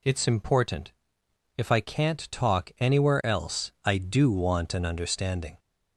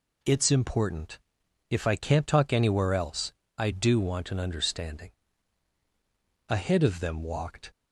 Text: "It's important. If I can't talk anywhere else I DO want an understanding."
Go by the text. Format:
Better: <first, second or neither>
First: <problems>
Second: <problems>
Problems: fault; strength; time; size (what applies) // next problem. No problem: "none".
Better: first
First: none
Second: pauses between "else" and "I"; slight; at 3.3 s; 0.24 s long // goes on to say "Ahead of them walked"; noticeable; from 6.4 s on; 1.2 s long